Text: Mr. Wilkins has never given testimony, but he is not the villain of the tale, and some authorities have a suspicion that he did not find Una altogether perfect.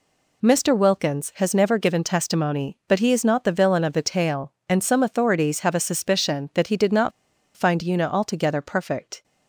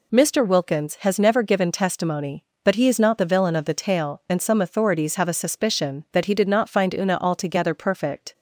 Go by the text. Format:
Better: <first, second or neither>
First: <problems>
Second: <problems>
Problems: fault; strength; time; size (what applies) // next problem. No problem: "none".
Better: second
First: pauses between "not" and "find"; at 7.1 s; 0.43 s long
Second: none